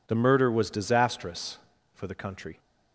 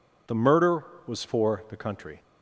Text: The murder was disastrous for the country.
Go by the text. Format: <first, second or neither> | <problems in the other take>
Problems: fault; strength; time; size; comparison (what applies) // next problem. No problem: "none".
first | skips "disastrous"; at 1.2 s